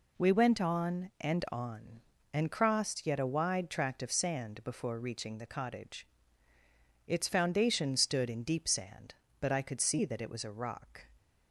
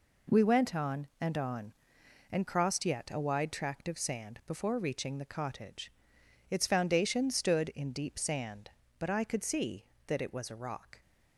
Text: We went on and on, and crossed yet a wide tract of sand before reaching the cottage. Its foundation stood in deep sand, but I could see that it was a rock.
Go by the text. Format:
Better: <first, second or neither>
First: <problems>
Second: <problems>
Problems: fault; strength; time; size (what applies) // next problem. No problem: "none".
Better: neither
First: none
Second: none